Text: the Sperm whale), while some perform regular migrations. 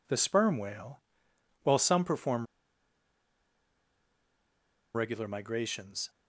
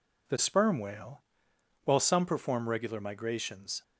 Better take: second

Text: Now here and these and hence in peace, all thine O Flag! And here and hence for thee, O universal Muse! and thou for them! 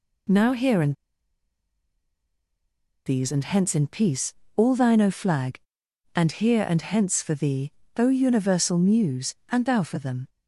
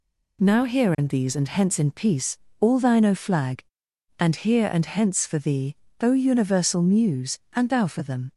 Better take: second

